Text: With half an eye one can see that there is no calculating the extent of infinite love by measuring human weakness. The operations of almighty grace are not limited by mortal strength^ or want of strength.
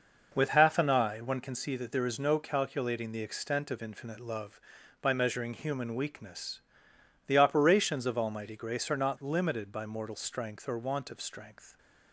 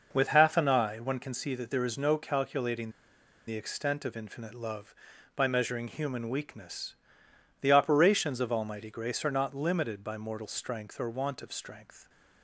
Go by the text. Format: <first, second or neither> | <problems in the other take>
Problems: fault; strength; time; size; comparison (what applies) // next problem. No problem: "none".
first | pauses between "calculating" and "the"; noticeable; at 2.8 s; 0.57 s long